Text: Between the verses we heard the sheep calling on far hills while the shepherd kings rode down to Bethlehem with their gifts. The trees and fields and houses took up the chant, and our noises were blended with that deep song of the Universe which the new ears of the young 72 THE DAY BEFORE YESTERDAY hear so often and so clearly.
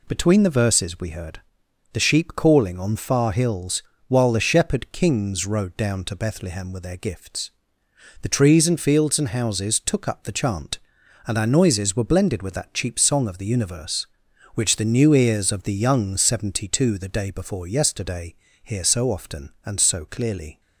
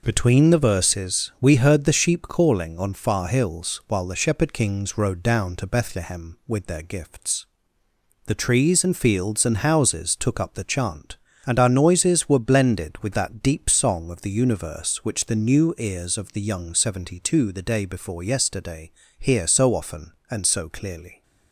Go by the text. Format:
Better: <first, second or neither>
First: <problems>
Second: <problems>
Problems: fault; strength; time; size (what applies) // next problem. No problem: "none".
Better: second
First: pauses between "heard" and "the"; noticeable; at 1.4 s; 0.54 s long // pauses between "hills" and "while"; slight; at 3.8 s; 0.26 s long // says "cheap" for "deep"; at 12.7 s // pauses between "YESTERDAY" and "hear"; slight; at 18.3 s; 0.28 s long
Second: pauses between "YESTERDAY" and "hear"; slight; at 18.9 s; 0.26 s long